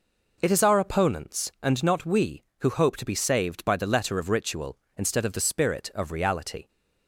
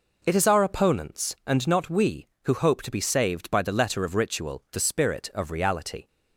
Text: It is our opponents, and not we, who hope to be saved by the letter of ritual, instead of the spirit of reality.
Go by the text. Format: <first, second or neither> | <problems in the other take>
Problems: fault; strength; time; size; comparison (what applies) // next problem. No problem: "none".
first | skips "instead of"; at 4.6 s